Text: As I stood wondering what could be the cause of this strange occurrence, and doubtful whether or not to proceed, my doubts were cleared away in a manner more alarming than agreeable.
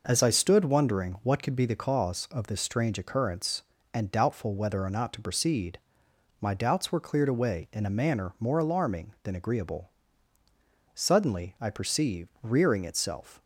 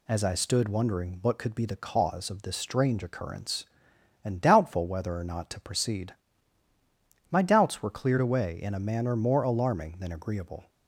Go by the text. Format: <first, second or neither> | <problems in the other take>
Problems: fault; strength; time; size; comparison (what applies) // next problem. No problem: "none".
second | goes on to say "Suddenly I perceived rearing itself"; strong; from 10.9 s on; 2.4 s long